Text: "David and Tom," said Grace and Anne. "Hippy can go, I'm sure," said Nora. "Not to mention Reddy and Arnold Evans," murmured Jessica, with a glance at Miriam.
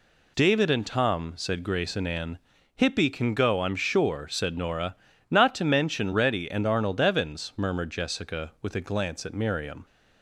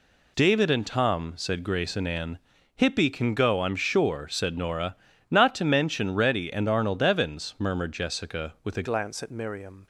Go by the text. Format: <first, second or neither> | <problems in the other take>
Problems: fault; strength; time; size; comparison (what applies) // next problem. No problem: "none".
first | changes voice at "glance"; from 8.8 s on; 1.0 s long